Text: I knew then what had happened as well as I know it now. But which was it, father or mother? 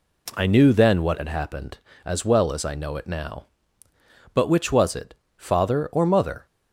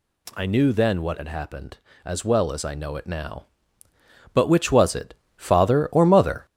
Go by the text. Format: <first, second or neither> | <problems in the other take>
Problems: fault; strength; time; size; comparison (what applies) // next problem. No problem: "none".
first | gets louder; throughout; 6.5 dB